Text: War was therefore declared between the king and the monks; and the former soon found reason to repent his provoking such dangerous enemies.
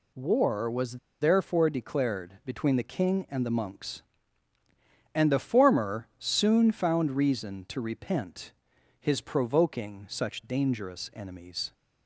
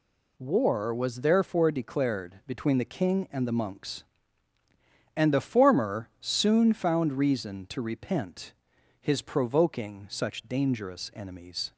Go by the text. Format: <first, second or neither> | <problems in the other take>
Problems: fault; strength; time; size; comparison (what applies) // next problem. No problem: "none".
second | pauses between "was" and "therefore"; slight; at 0.9 s; 0.24 s long // pauses between "repent" and "his"; noticeable; at 8.5 s; 0.48 s long; noticeable in the second